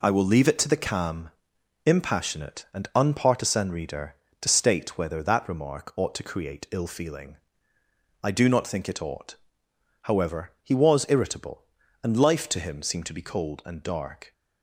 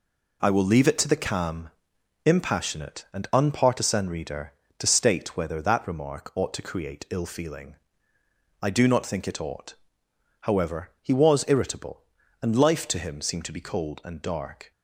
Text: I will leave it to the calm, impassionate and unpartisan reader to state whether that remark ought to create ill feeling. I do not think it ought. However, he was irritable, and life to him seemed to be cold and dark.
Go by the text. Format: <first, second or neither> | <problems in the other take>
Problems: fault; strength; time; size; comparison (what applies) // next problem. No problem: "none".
neither | none